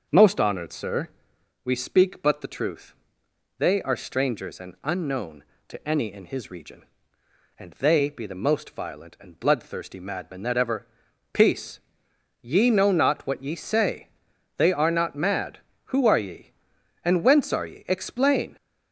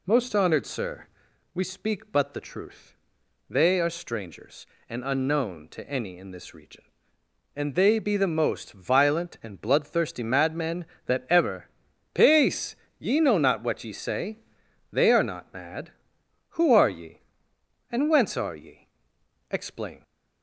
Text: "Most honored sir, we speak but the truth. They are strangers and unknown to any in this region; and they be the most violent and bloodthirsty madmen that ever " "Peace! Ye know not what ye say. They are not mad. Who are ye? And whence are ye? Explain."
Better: second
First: starts louder than the rest; until 1.6 s; 6.5 dB // says "his" for "this"; at 6.2 s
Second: none

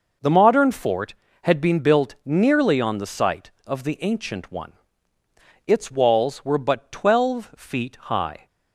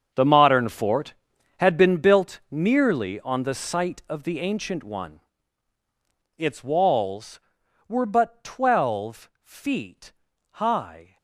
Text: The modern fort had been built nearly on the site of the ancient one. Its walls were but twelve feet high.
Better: first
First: none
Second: gets quieter; strong; throughout; 15.5 dB // pauses between "feet" and "high"; at 10.1 s; 0.40 s long

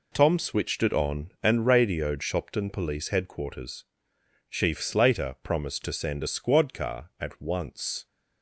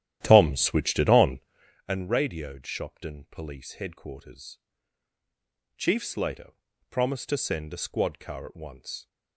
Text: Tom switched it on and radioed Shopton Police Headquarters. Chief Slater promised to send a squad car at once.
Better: first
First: none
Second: starts louder than the rest; strong; until 1.8 s; 12 dB // pauses between "Slater" and "promised"; at 6.5 s; 0.38 s long

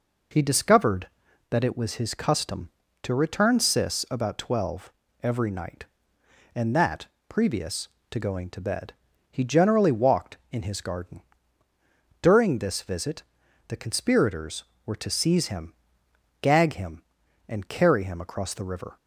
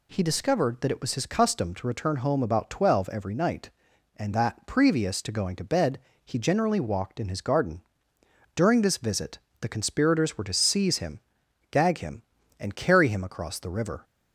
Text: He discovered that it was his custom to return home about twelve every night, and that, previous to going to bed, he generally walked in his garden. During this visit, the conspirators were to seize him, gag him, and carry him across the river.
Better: second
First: says "sis" for "home"; at 3.5 s // pauses between "twelve" and "every"; slight; at 4.8 s; 0.32 s long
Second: none

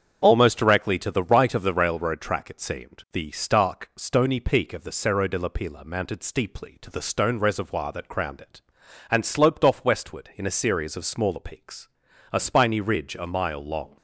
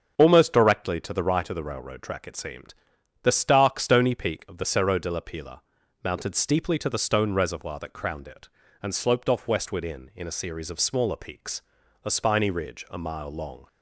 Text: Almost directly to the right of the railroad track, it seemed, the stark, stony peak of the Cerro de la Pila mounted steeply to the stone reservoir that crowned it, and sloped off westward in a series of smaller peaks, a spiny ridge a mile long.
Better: first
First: starts louder than the rest; strong; until 1.2 s; 7.5 dB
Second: starts louder than the rest; strong; until 1.2 s; 7.5 dB // pauses between "Pila" and "mounted"; at 5.6 s; 0.42 s long // says "in" twice; at 10.1 s

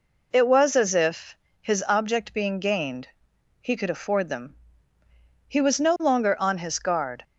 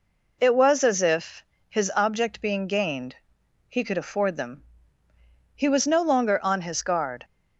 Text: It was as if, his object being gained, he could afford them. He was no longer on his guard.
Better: neither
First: none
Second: none

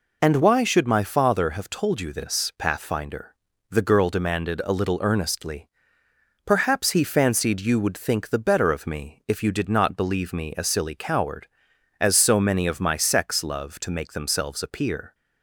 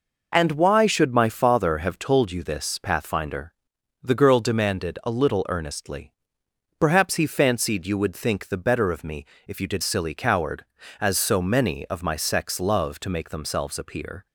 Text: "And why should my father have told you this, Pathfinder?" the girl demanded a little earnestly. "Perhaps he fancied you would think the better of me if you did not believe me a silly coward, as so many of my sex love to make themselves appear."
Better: first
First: none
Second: pauses between "me" and "if"; slight; at 9.2 s; 0.20 s long // skips "not believe me a"; at 9.8 s

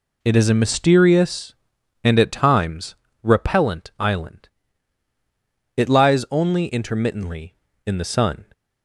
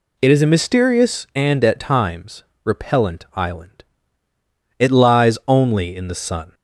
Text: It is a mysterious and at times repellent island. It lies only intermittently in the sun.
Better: first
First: pauses between "times" and "repellent"; slight; at 2.9 s; 0.28 s long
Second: pauses between "times" and "repellent"; slight; at 2.4 s; 0.20 s long // skips "intermittently"; at 5.9 s

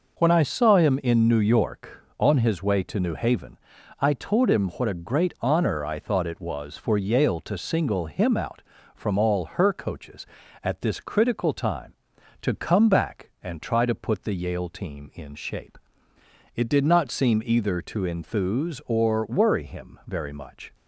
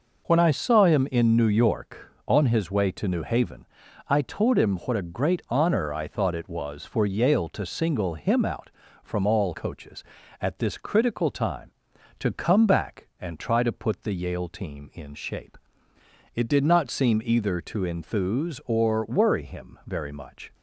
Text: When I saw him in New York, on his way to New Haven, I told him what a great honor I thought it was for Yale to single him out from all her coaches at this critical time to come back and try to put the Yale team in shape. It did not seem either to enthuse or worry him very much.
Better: first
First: none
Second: skips "her"; at 9.5 s

